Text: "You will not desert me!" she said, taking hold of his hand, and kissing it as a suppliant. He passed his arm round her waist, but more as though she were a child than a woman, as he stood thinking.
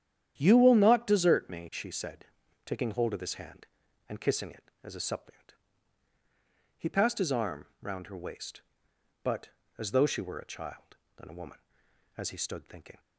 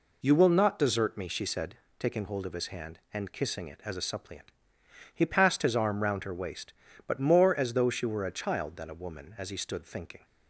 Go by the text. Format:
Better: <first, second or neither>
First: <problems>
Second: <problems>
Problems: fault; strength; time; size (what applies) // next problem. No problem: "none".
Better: second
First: starts louder than the rest; strong; until 1.3 s; 10 dB // pauses between "arm" and "round"; slight; at 7.6 s; 0.16 s long // skips "more"; at 9.6 s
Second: none